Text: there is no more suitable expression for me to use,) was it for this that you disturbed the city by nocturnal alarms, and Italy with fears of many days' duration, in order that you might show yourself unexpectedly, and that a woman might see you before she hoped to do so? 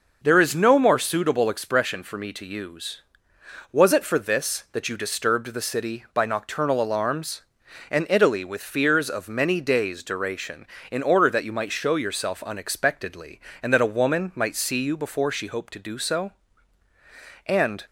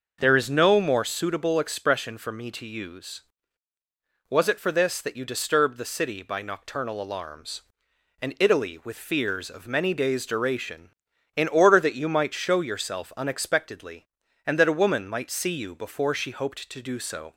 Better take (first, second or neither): second